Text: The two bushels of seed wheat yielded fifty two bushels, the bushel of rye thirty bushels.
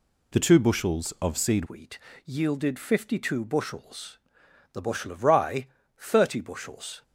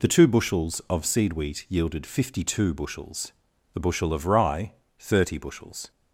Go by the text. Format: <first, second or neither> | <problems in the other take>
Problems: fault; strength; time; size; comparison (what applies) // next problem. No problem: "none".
second | changes voice at "wheat"; from 1.6 s on; 5.4 s long // pauses between "wheat" and "yielded"; slight; at 1.9 s; 0.26 s long // pauses between "rye" and "thirty"; slight; at 5.6 s; 0.32 s long; slight in the second